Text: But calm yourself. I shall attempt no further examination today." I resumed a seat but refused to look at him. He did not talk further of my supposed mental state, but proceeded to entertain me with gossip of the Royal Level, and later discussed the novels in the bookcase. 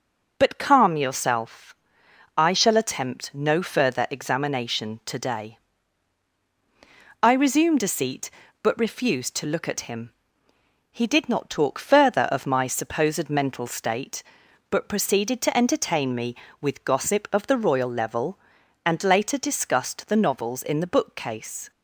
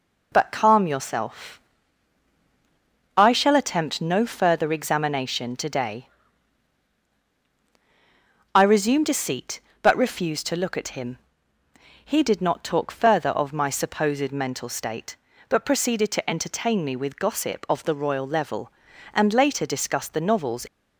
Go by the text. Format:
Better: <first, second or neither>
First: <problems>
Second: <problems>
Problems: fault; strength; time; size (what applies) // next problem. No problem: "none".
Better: first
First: none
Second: stops before "in the bookcase"; at 20.6 s